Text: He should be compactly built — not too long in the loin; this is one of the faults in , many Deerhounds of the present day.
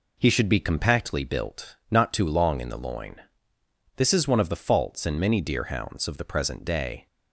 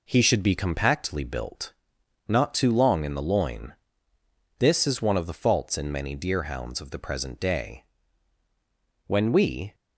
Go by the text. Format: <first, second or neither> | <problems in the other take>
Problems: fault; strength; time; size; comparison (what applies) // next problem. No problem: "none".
first | goes on to say "When we"; noticeable; from 9.0 s on; 0.66 s long